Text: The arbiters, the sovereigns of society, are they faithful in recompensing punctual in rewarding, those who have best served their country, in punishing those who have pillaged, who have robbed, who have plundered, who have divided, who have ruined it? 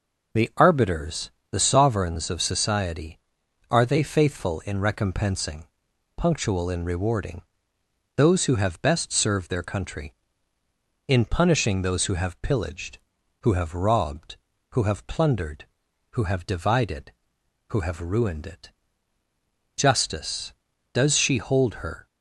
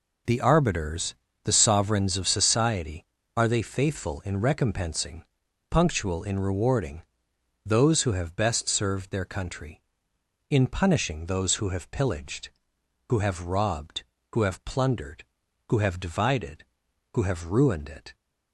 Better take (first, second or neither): second